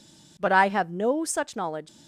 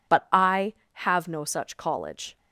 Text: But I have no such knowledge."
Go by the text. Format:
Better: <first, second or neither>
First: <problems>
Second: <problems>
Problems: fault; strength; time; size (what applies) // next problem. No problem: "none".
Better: first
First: none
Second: says "college" for "knowledge"; at 1.7 s